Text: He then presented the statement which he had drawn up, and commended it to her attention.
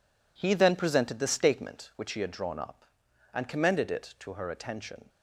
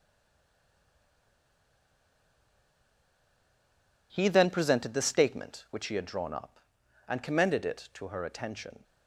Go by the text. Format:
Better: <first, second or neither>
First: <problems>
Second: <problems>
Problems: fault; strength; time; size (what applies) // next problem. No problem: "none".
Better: first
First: none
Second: stays silent before the first word; strong; until 4.1 s; 4.1 s long